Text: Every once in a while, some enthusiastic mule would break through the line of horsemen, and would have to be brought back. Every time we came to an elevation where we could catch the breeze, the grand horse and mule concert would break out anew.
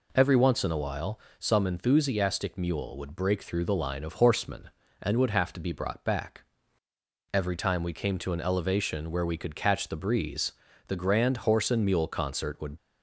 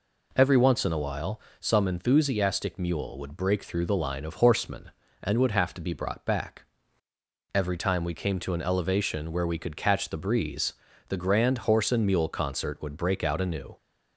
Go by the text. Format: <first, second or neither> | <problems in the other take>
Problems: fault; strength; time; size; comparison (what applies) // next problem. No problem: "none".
second | stops before "break out anew"; at 12.7 s